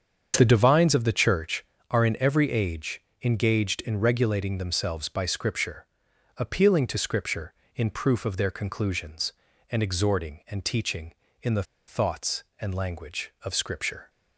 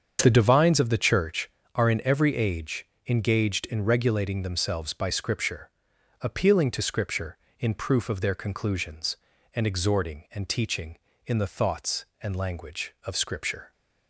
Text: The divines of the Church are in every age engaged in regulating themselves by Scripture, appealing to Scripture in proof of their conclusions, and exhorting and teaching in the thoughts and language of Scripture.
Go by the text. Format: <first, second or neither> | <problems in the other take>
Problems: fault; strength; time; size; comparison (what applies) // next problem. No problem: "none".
second | starts louder than the rest; strong; until 1.3 s; 7.5 dB; strong in the second // pauses between "age" and "engaged"; slight; at 3.0 s; 0.22 s long; slight in the second // pauses between "the" and "thoughts"; slight; at 11.6 s; 0.24 s long